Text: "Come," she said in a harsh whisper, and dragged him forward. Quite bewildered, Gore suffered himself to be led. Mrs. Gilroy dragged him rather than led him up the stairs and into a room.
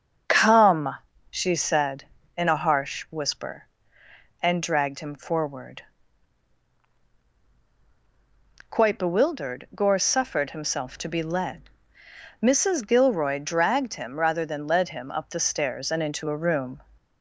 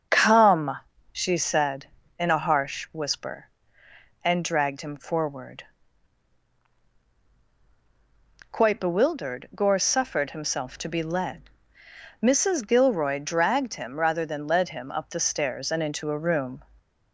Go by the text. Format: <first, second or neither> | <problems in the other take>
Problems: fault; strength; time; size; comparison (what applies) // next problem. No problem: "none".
neither | starts louder than the rest; the same in both